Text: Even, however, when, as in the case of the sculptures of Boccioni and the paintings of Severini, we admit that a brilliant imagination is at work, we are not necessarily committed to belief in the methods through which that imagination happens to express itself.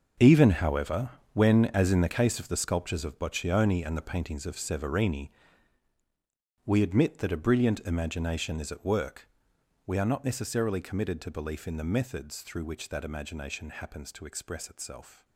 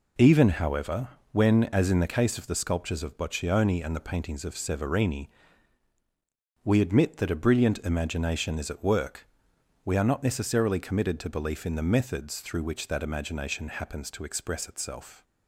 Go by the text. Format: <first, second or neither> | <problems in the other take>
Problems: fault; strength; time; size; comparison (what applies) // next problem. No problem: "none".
second | gets quieter; strong; throughout; 13 dB